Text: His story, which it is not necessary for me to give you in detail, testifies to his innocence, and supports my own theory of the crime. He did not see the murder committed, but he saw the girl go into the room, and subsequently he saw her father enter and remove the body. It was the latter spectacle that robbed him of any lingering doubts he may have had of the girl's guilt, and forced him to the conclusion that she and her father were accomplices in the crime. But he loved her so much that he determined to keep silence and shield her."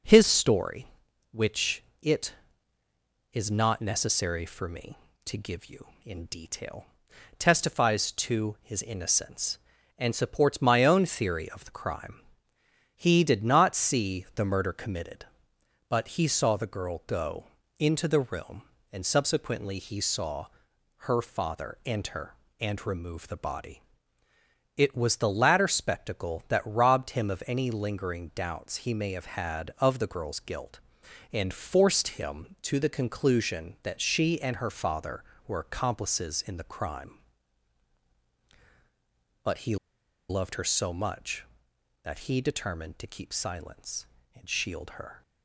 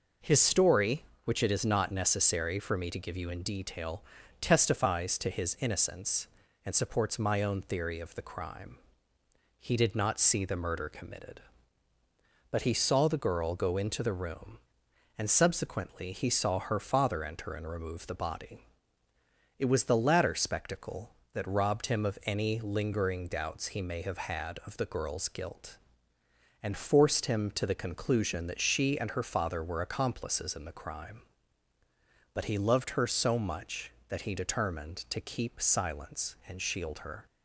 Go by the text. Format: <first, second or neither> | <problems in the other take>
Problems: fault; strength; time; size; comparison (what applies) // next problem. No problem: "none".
second | pauses between "which" and "it"; slight; at 1.8 s; 0.20 s long // pauses between "go" and "into"; slight; at 17.4 s; 0.32 s long // pauses between "saw" and "her"; noticeable; at 20.4 s; 0.58 s long // pauses between "he" and "loved"; noticeable; at 39.7 s; 0.52 s long